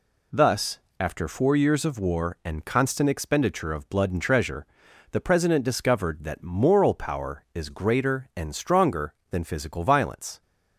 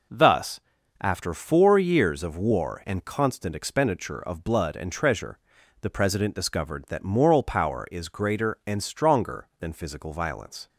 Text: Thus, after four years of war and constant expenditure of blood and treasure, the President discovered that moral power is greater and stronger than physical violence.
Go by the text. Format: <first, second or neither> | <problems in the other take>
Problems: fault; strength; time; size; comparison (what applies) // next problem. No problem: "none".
neither | none